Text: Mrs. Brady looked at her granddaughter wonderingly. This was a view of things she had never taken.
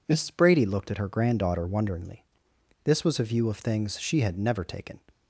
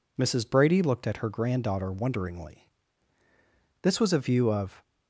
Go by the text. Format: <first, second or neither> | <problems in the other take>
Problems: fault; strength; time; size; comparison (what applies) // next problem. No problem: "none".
first | stops before "things she had never taken"; at 4.8 s